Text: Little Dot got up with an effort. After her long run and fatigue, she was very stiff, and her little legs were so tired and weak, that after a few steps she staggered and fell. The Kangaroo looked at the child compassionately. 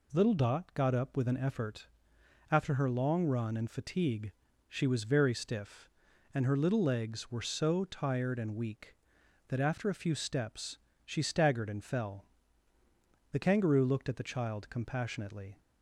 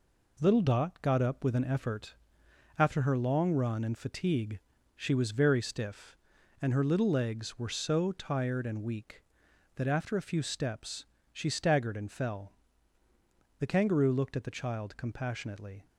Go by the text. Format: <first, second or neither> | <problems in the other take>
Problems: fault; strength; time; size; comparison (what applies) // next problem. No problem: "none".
first | gets quieter; noticeable; throughout; 6 dB // pauses between "steps" and "she"; slight; at 11.0 s; 0.26 s long; slight in the first